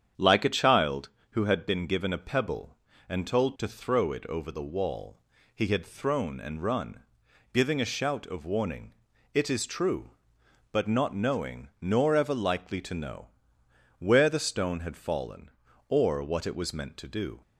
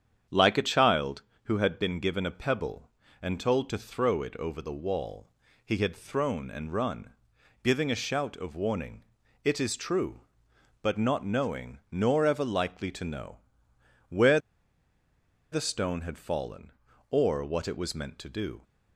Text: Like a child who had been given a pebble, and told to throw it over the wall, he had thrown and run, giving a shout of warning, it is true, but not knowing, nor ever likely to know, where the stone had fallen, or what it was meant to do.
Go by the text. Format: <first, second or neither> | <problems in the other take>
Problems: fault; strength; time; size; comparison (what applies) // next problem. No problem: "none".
first | starts louder than the rest; strong; until 1.5 s; 8.5 dB; strong in the first // pauses between "where" and "the"; at 14.3 s; 1.1 s long